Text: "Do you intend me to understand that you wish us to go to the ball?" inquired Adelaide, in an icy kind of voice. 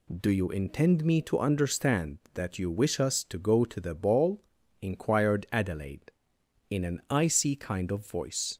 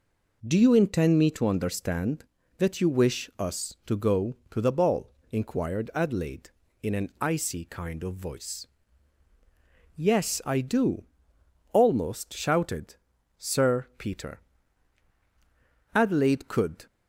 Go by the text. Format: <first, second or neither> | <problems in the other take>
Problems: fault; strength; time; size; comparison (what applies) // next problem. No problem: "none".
first | goes on to say "Yes I do almost shouted Sir Peter Adelaide could"; strong; from 9.9 s on; 6.9 s long